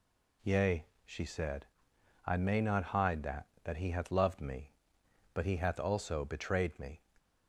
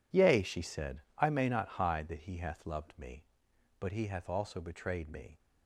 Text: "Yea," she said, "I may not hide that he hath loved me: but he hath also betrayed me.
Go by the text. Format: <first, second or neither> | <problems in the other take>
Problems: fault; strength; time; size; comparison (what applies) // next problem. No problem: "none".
second | says "that" twice; at 3.6 s